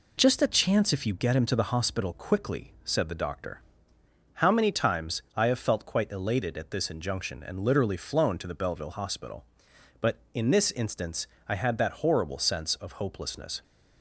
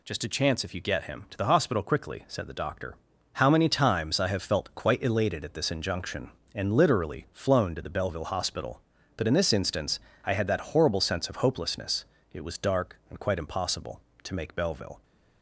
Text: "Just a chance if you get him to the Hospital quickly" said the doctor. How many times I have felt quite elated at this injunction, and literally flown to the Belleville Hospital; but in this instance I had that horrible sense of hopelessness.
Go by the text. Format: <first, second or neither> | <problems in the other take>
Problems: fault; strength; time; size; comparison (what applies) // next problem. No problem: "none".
first | pauses between "instance" and "I"; slight; at 9.9 s; 0.26 s long; slight in the first // goes on to say "It was dark and quite impossible to make Belleville"; strong; from 12.3 s on; 2.7 s long